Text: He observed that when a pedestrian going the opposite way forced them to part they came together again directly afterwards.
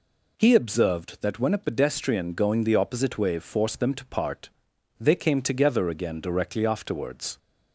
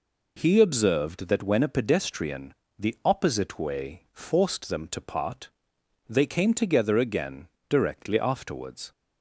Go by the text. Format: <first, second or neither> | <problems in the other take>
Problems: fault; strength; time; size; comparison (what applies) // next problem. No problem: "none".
first | skips "going"; at 2.6 s // pauses between "part" and "they"; noticeable; at 5.4 s; 0.58 s long; noticeable in the first // pauses between "again" and "directly"; slight; at 7.4 s; 0.22 s long